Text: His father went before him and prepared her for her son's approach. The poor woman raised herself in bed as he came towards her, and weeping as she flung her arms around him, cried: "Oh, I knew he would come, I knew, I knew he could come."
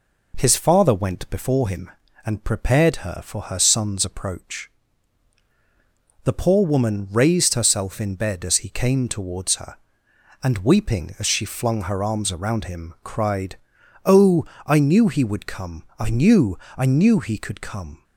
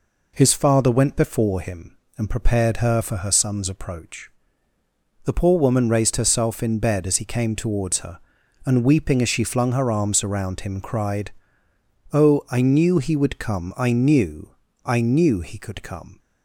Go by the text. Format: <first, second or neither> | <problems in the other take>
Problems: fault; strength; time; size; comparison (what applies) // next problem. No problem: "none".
neither | none